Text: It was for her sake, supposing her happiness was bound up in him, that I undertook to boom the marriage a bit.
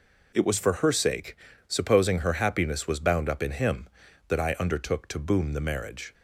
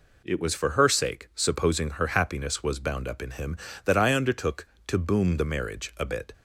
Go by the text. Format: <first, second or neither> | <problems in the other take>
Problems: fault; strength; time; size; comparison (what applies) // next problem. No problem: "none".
second | stops before "a bit"; at 6.1 s